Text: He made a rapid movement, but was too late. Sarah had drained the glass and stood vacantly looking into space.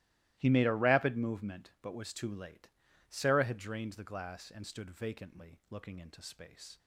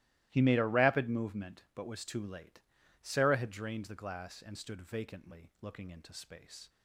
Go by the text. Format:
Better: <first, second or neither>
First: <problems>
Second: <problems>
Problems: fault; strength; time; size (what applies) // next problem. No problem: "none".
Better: neither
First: starts louder than the rest; strong; until 1.3 s; 17 dB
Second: starts louder than the rest; strong; until 1.3 s; 16.5 dB